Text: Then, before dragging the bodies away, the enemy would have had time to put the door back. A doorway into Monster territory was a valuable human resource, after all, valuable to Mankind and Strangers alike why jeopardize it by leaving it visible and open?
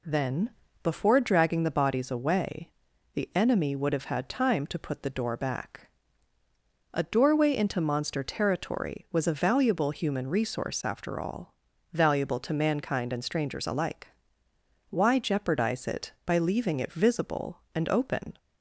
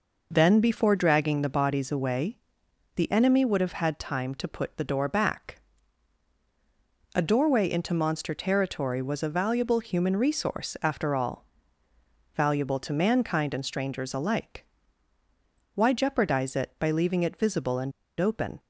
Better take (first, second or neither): first